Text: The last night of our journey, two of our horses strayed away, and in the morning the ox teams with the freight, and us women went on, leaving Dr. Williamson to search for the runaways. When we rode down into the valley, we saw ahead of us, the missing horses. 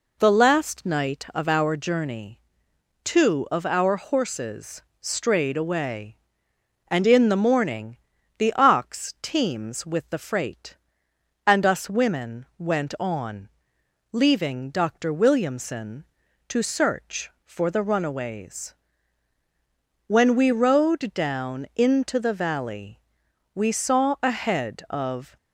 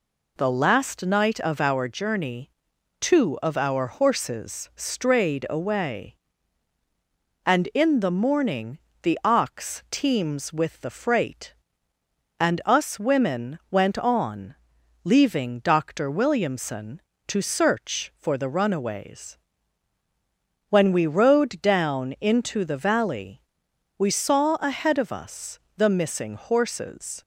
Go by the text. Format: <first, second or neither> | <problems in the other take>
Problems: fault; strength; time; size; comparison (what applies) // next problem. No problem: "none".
second | pauses between "horses" and "strayed"; slight; at 4.8 s; 0.18 s long // pauses between "morning" and "the"; at 7.9 s; 0.40 s long; slight in the second // stops before "us the missing horses"; at 25.3 s